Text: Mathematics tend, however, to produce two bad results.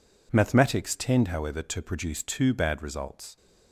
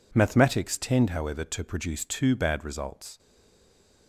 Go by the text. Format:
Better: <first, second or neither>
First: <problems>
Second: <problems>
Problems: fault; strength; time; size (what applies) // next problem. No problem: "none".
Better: first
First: none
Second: stays silent after the last word; slight; from 3.1 s on; 0.9 s long